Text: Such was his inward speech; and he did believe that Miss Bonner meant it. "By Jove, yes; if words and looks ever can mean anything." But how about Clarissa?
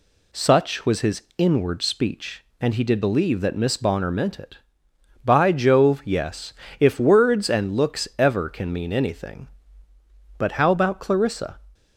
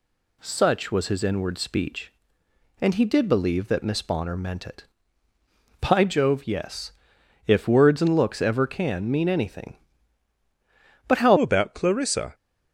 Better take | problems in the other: first | changes voice at "about"; from 11.3 s on; 1.0 s long

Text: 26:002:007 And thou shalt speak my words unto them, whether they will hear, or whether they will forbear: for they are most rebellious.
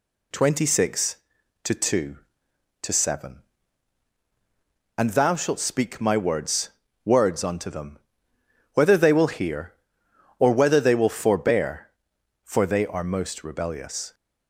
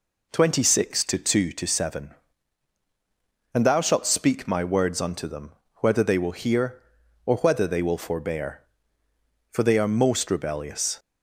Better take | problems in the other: second | says "words" twice; at 7.0 s

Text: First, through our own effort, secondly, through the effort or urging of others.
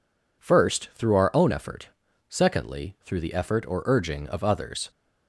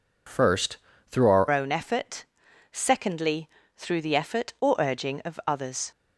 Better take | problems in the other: first | changes voice at "own"; from 1.5 s on; 4.4 s long

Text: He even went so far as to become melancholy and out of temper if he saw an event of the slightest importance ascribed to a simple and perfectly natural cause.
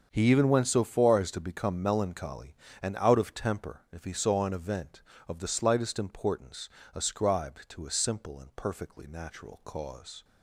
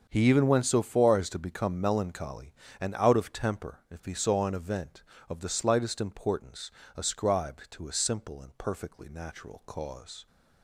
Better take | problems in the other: neither | starts louder than the rest; the same in both // pauses between "importance" and "ascribed"; slight; the same in both

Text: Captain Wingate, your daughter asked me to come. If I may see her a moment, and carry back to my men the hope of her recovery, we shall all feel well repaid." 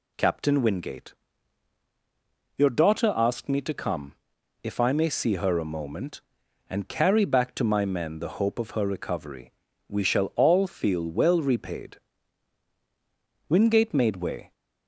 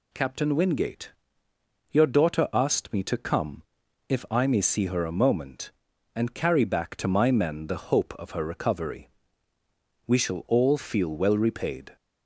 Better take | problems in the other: second | goes on to say "Wingate made way"; noticeable; from 13.4 s on; 1.0 s long

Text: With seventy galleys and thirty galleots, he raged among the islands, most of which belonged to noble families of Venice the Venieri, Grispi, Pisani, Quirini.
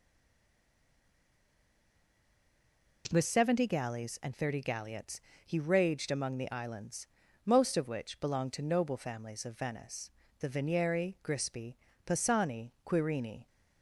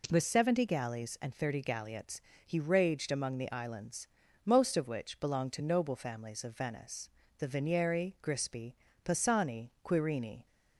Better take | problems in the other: second | stays silent before the first word; strong; until 3.0 s; 3.0 s long // pauses between "Venice" and "the"; slight; at 10.1 s; 0.30 s long; slight in the second

